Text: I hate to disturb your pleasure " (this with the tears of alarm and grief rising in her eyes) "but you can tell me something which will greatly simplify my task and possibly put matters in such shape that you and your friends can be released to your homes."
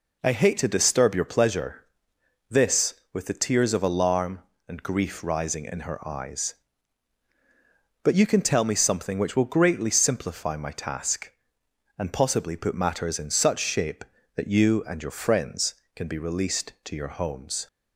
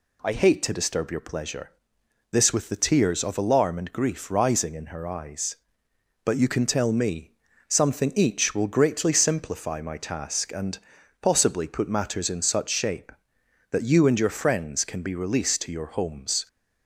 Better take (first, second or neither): first